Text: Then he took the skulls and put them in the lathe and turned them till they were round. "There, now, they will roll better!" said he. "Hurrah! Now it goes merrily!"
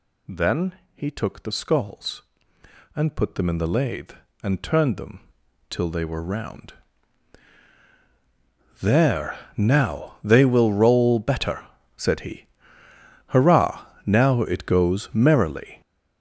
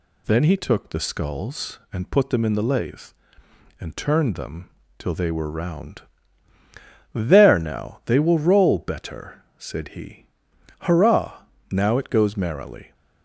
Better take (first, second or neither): second